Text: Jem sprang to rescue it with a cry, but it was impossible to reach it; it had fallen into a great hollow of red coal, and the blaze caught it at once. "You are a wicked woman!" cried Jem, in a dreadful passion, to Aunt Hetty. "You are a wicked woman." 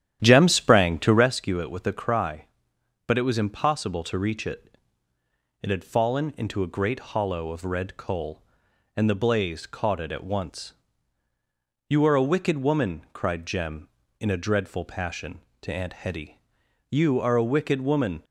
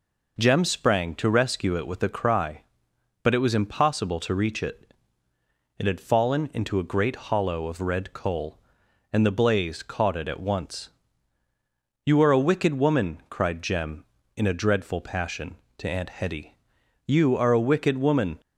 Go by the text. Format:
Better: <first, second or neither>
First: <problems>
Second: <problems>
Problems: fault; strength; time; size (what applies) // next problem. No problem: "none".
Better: second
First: starts louder than the rest; strong; until 1.4 s; 11 dB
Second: none